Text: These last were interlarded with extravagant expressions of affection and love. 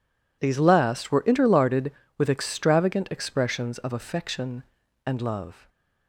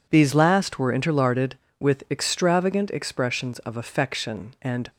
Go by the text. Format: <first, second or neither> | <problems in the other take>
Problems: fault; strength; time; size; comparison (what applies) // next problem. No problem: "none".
first | stops before "love"; at 4.8 s